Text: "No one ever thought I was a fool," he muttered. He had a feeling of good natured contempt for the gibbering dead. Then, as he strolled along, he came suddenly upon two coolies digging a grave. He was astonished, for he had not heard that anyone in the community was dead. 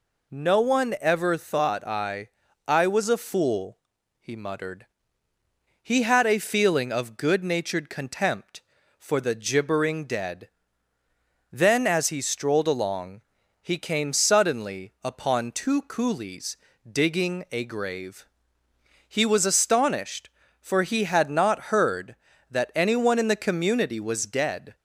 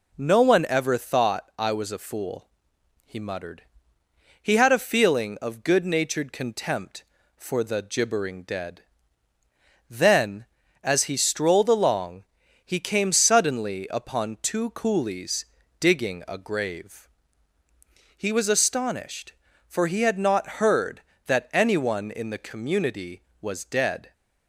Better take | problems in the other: second | says "I" twice; at 2.6 s // pauses between "coolies" and "digging"; slight; at 16.5 s; 0.32 s long; slight in the second

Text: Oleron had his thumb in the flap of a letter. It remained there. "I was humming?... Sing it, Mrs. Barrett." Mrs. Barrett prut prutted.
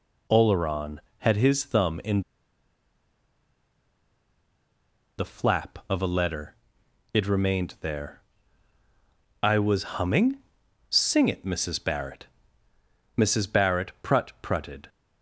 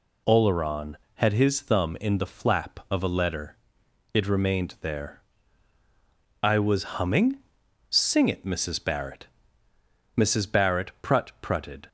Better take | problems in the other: second | pauses between "in" and "the"; strong; at 2.2 s; 2.9 s long

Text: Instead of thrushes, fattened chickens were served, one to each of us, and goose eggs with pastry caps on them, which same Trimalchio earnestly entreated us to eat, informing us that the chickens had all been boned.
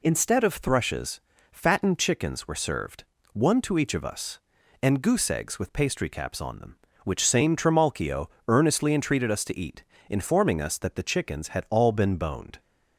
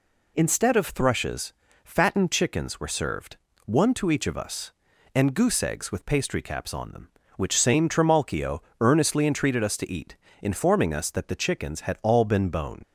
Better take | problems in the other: first | pauses between "Trimalchio" and "earnestly"; slight; at 8.6 s; 0.20 s long; slight in the first // leaves "boned" unfinished; at 12.8 s; 80 ms

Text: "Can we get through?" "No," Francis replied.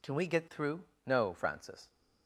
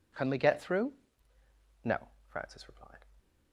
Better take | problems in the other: second | stops before "replied"; at 1.8 s

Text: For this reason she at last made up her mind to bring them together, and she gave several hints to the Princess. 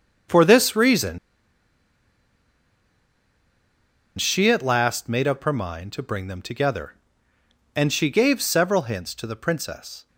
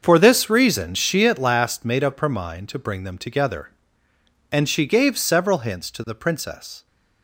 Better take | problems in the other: second | starts louder than the rest; until 4.3 s; 6.5 dB; also in the second // pauses between "reason" and "she"; strong; at 1.1 s; 3.0 s long

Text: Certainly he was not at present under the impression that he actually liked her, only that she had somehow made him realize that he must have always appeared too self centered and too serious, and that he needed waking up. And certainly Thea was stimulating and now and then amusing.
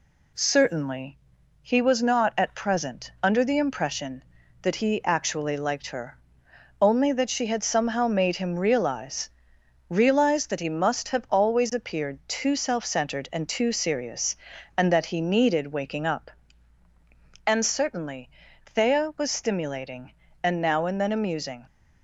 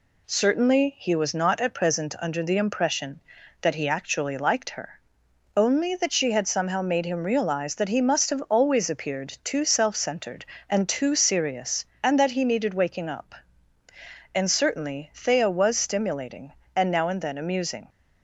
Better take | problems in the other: second | pauses between "Certainly" and "he"; at 1.1 s; 0.42 s long // says "realize" twice; at 9.9 s // pauses between "certainly" and "Thea"; at 18.2 s; 0.38 s long

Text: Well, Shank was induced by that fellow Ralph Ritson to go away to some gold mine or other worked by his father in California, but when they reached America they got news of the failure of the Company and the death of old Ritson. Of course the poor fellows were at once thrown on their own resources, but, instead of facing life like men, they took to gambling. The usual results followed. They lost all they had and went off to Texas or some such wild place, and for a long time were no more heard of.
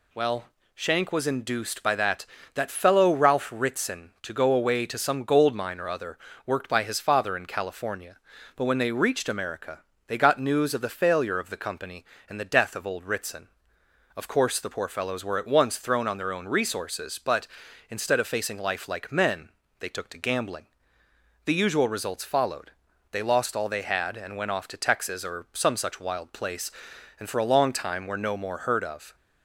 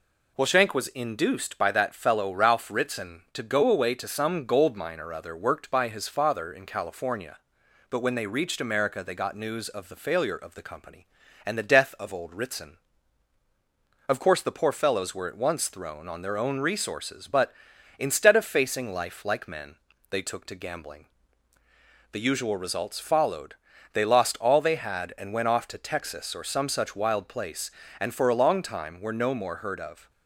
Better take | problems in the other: second | says "that" twice; at 2.5 s // pauses between "other" and "worked"; slight; at 6.1 s; 0.28 s long // pauses between "America" and "they"; slight; at 9.7 s; 0.28 s long

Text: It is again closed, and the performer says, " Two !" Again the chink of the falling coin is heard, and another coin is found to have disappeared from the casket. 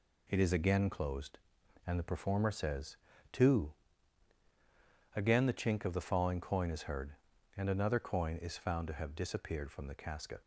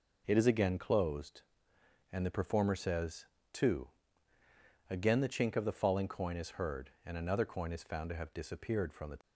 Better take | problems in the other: first | stops before "casket"; at 9.2 s

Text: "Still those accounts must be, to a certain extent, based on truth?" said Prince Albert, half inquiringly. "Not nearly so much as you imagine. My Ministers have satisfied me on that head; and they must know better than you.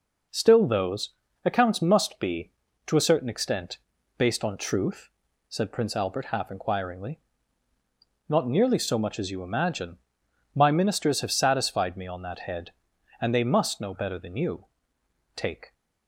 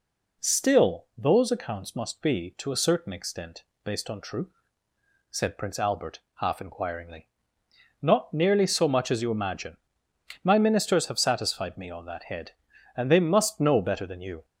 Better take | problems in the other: second | pauses between "those" and "accounts"; slight; at 1.1 s; 0.32 s long // goes on to say "Take"; slight; from 15.3 s on; 0.38 s long

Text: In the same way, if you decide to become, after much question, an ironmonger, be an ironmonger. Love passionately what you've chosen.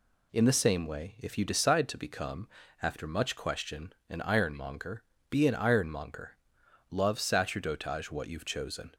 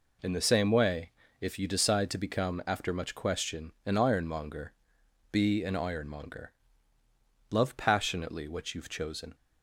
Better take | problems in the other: second | says "sacerdotage" for "passionately"; at 7.1 s

